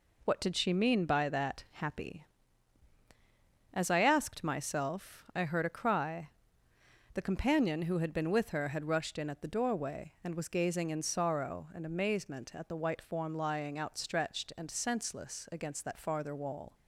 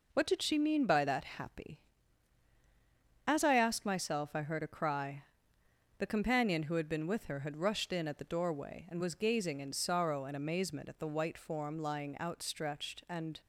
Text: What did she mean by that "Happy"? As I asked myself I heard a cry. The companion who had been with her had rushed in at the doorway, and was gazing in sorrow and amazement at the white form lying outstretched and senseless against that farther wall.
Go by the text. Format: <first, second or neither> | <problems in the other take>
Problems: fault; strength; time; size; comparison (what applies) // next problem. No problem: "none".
first | stops before "senseless against that farther wall"; at 13.4 s